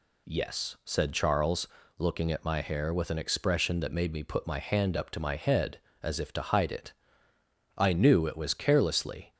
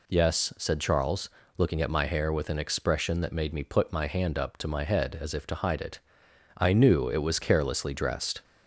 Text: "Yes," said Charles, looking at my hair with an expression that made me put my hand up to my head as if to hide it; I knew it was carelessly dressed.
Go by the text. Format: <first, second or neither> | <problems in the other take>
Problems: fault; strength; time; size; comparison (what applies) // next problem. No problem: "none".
second | stops before "dressed"; at 9.3 s